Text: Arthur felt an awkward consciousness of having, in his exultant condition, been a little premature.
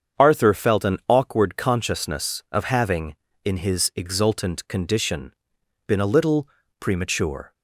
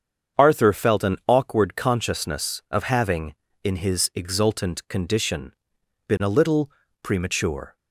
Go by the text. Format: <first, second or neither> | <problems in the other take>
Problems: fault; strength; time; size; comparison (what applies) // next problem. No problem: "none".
neither | starts louder than the rest; strong; the same in both // pauses between "little" and "premature"; slight; the same in both